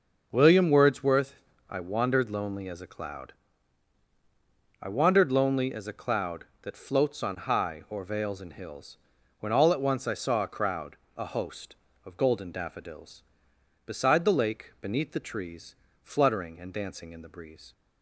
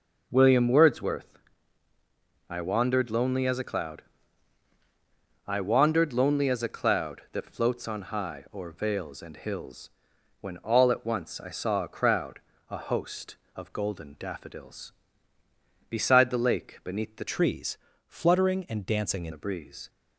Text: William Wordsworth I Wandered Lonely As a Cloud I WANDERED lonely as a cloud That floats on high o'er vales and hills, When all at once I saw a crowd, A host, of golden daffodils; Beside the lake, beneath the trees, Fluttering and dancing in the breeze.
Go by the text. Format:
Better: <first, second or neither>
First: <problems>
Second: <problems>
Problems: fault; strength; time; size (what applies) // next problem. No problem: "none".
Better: first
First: pauses between "Wordsworth" and "I"; slight; at 1.3 s; 0.34 s long // pauses between "Cloud" and "I"; strong; at 3.3 s; 1.4 s long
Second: pauses between "Wordsworth" and "I"; at 1.3 s; 1.1 s long // pauses between "Cloud" and "I"; strong; at 4.0 s; 1.4 s long // changes voice from "trees" to "in"; from 17.2 to 19.3 s; 2.1 s long